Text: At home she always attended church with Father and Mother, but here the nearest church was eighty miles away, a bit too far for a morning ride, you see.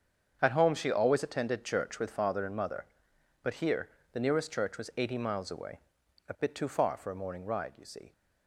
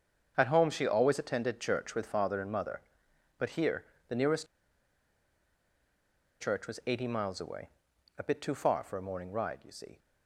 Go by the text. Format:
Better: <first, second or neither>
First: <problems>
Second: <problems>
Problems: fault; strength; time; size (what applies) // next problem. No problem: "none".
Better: first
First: starts louder than the rest; until 1.4 s; 7 dB // pauses between "here" and "the"; slight; at 3.8 s; 0.24 s long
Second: starts louder than the rest; until 1.3 s; 7 dB // pauses between "here" and "the"; slight; at 3.8 s; 0.24 s long // pauses between "nearest" and "church"; strong; at 4.4 s; 1.9 s long